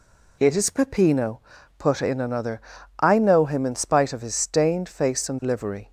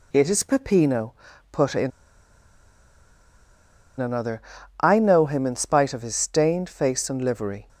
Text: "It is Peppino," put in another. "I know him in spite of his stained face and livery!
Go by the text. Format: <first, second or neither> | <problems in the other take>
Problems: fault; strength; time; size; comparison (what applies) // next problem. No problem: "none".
first | pauses between "in" and "another"; strong; at 1.9 s; 2.0 s long